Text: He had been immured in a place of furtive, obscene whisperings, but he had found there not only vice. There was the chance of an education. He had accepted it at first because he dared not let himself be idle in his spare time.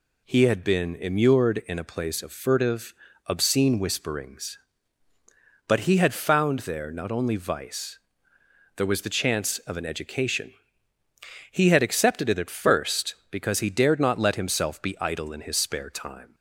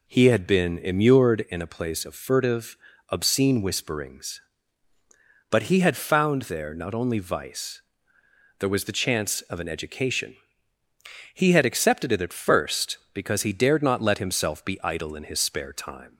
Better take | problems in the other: first | starts louder than the rest; slight; until 1.5 s; 3 dB

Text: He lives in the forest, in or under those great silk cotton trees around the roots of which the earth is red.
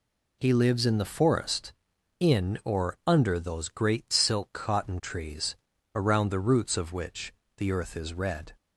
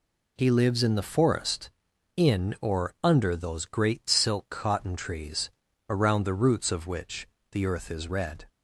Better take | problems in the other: neither | pauses between "trees" and "around"; the same in both // pauses between "which" and "the"; slight; the same in both

